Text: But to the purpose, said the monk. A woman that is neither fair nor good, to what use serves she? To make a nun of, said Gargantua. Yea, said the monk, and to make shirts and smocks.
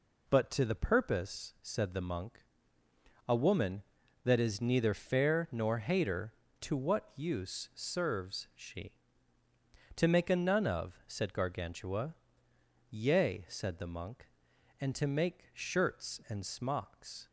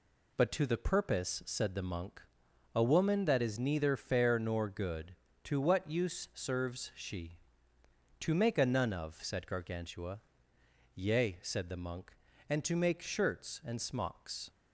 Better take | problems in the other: second | says "hater" for "good"; at 5.7 s

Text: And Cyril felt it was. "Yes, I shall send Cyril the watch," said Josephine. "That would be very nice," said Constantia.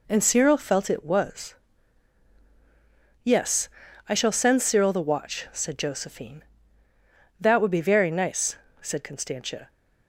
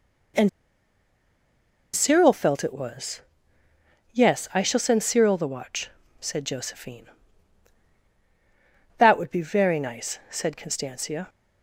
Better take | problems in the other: first | pauses between "And" and "Cyril"; strong; at 0.4 s; 1.4 s long

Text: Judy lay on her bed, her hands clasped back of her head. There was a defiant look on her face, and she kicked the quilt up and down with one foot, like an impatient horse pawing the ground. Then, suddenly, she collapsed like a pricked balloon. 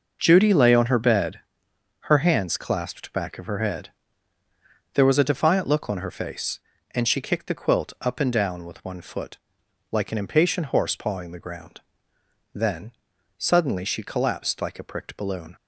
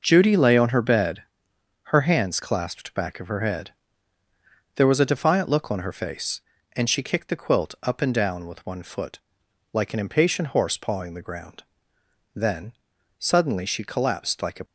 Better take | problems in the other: first | stops before "pricked balloon"; at 14.6 s

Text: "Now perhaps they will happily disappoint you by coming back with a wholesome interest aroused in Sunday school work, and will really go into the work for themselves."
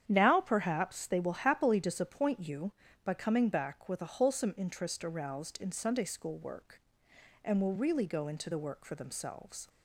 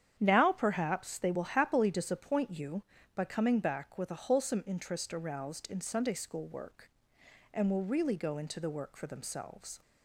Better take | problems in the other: neither | starts louder than the rest; strong; the same in both

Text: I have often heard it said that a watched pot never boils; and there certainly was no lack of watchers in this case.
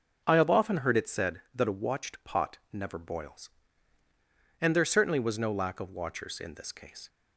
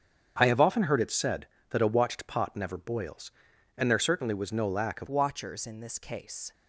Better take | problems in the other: first | starts louder than the rest; strong; until 1.3 s; 7.5 dB // changes voice at "watchers"; from 5.0 s on; 1.5 s long

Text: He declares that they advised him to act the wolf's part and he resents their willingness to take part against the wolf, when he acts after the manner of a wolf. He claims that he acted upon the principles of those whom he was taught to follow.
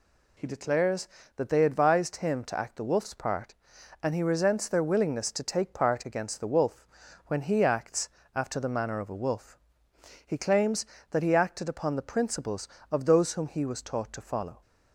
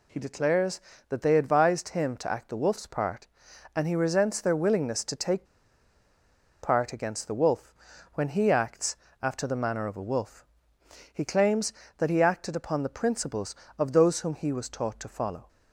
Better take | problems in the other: first | pauses between "take" and "part"; at 5.4 s; 1.1 s long // pauses between "acts" and "after"; slight; at 8.9 s; 0.24 s long; slight in the first

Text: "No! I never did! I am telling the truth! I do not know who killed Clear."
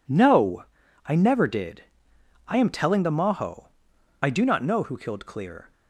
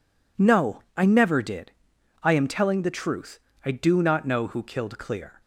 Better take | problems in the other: second | says "maho" for "truth"; at 3.1 s

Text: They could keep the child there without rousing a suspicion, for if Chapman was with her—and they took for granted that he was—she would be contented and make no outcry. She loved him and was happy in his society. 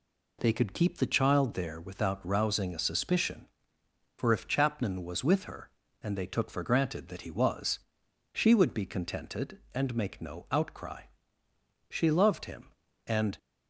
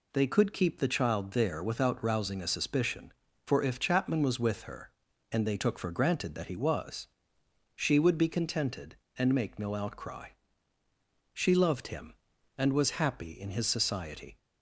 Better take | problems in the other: second | stops before "was happy in his society"; at 13.3 s

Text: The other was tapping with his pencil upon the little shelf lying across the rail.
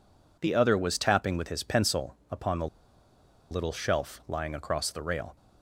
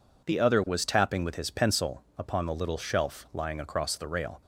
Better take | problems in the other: second | pauses between "the" and "little"; noticeable; at 2.6 s; 0.83 s long

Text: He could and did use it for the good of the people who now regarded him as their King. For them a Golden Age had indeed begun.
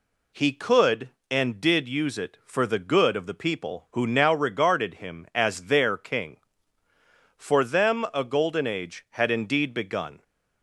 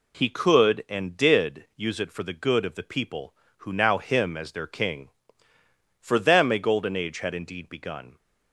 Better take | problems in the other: first | skips "regarded"; at 3.9 s

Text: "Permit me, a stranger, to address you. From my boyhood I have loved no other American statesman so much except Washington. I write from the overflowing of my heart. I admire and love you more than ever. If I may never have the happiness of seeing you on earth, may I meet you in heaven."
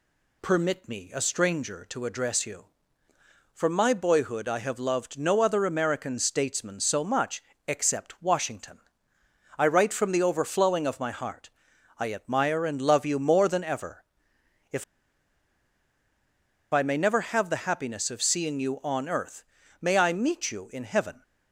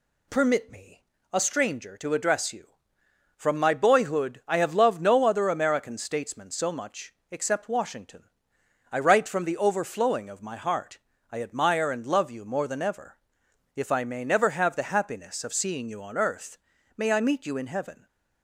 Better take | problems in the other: second | pauses between "much" and "except"; slight; at 7.4 s; 0.24 s long; slight in the second // pauses between "If" and "I"; strong; at 14.8 s; 1.8 s long

